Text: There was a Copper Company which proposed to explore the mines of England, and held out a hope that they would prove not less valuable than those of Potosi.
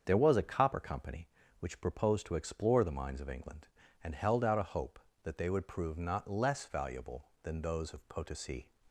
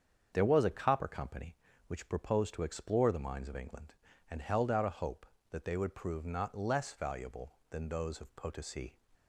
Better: neither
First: starts louder than the rest; strong; until 1.0 s; 7 dB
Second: starts louder than the rest; strong; until 1.3 s; 7 dB

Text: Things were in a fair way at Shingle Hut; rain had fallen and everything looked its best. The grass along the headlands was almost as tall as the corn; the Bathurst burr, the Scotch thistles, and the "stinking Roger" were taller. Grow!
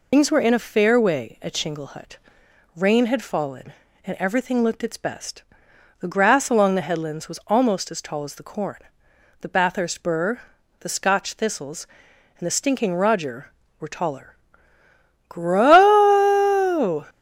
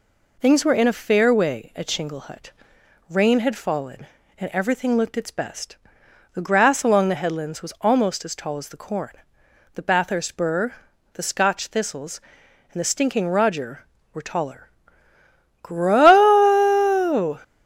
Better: second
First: loses the start of "Things"; at 0.1 s; 65 ms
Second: none

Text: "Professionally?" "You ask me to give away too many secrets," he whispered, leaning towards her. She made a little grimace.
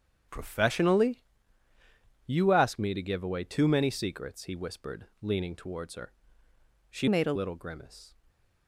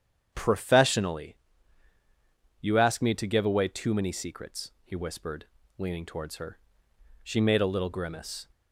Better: second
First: starts louder than the rest; strong; until 2.3 s; 7.5 dB // changes voice from "made" to "a"; from 7.0 to 7.3 s; 0.3 s long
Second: starts louder than the rest; strong; until 1.3 s; 8.5 dB

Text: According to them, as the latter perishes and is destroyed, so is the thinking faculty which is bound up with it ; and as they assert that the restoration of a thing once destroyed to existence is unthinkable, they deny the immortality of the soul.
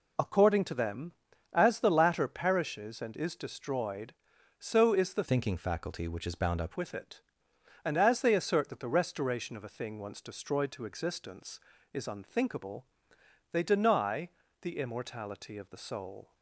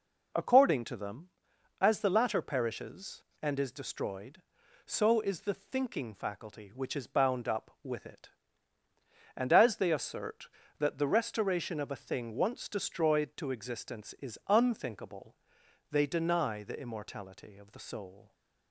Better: second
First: changes voice from "thinking" to "up"; from 5.2 to 6.7 s; 1.5 s long // pauses between "deny" and "the"; slight; at 14.2 s; 0.32 s long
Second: none

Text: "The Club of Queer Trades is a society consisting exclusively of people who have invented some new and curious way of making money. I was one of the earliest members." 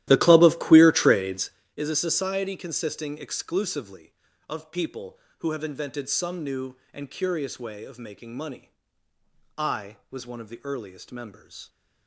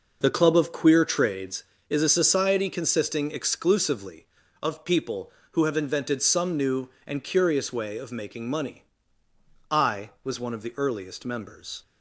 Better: second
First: starts louder than the rest; strong; until 1.7 s; 14 dB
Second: none

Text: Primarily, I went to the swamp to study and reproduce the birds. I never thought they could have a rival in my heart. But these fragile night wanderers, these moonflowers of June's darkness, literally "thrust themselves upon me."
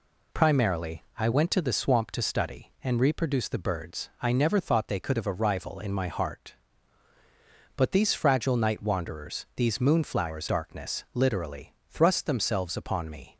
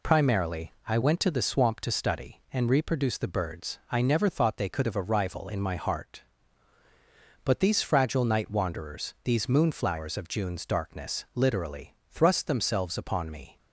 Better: second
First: skips "of June's"; at 10.4 s // pauses between "literally" and "thrust"; slight; at 11.7 s; 0.16 s long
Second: pauses between "literally" and "thrust"; slight; at 11.9 s; 0.16 s long

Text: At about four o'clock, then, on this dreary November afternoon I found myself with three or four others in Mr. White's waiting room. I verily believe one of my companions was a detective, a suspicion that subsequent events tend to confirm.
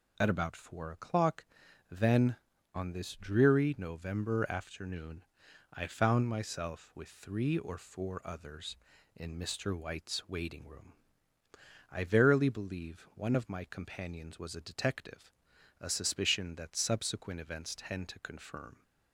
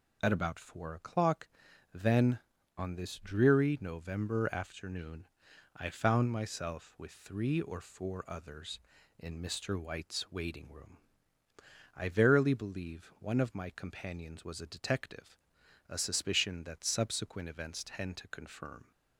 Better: neither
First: pauses between "afternoon" and "I"; noticeable; at 5.2 s; 0.48 s long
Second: pauses between "afternoon" and "I"; noticeable; at 5.2 s; 0.48 s long

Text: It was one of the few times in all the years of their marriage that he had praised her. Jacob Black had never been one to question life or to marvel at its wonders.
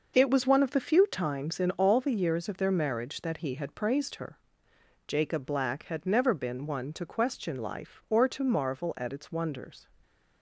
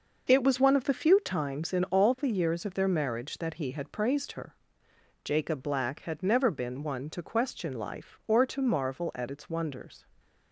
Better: neither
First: none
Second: none

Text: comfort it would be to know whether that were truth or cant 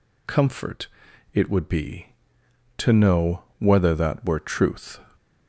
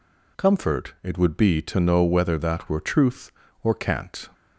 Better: second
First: pauses between "comfort" and "it"; noticeable; at 0.8 s; 0.46 s long // pauses between "know" and "whether"; slight; at 3.4 s; 0.16 s long // stops before "or cant"; at 5.1 s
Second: none

